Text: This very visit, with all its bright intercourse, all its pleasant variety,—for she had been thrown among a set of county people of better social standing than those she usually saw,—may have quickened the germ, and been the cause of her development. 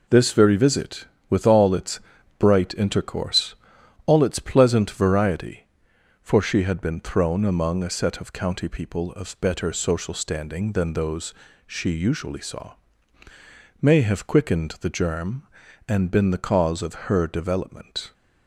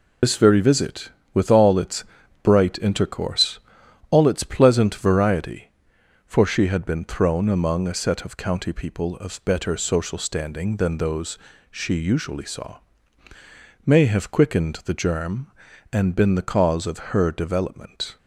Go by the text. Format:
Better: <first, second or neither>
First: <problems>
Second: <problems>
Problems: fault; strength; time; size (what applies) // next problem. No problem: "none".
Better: first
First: pauses between "its" and "bright"; at 1.9 s; 0.40 s long // pauses between "those" and "she"; slight; at 11.3 s; 0.34 s long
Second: loses the start of "This"; at 0.2 s; 95 ms // pauses between "its" and "bright"; at 2.0 s; 0.40 s long // pauses between "those" and "she"; slight; at 11.3 s; 0.34 s long